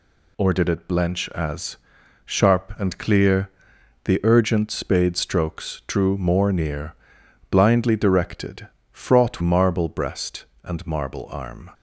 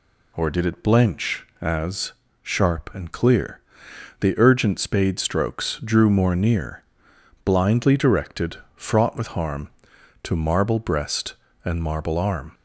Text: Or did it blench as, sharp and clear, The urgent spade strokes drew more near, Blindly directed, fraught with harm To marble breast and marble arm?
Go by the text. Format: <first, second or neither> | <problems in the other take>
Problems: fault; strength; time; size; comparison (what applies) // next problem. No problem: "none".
second | skips "with harm To"; at 9.4 s